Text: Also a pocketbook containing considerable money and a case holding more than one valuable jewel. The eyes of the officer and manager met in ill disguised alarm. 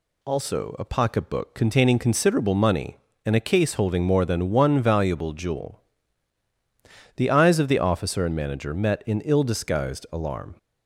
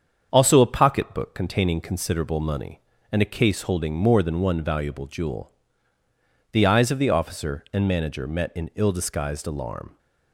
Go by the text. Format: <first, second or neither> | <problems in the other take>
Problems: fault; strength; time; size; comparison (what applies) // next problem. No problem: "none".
first | gets quieter; throughout; 3.5 dB